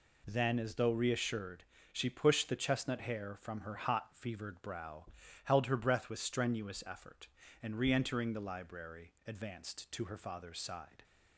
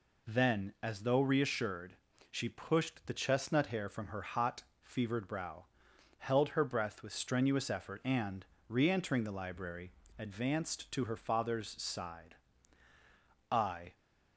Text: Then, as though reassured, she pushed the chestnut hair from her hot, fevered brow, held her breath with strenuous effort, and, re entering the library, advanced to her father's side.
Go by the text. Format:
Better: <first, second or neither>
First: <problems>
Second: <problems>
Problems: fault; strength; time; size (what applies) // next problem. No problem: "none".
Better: first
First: none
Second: goes on to say "I"; slight; from 13.5 s on; 0.44 s long